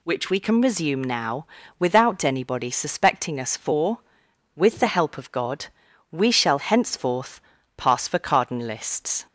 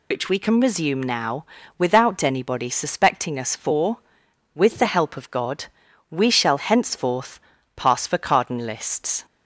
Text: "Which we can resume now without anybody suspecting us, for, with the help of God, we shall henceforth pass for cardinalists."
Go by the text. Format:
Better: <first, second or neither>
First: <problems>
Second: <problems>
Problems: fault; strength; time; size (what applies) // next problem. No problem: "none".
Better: first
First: pauses between "now" and "without"; slight; at 1.4 s; 0.32 s long // pauses between "henceforth" and "pass"; slight; at 7.3 s; 0.36 s long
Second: loses the start of "Which"; at 0.1 s; 75 ms // pauses between "now" and "without"; slight; at 1.4 s; 0.32 s long // pauses between "henceforth" and "pass"; slight; at 7.3 s; 0.36 s long